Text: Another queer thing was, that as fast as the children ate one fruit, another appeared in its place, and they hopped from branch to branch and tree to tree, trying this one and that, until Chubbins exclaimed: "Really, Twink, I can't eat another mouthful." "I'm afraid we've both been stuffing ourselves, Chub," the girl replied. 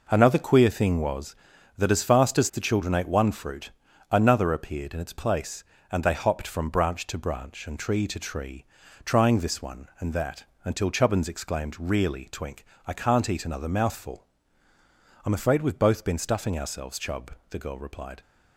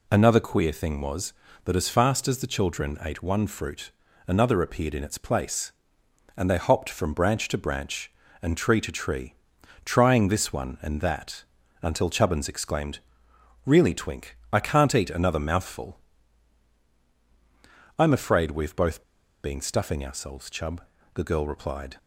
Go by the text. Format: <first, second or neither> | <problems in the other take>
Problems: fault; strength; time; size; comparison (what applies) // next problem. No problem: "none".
first | pauses between "both" and "been"; at 19.0 s; 0.40 s long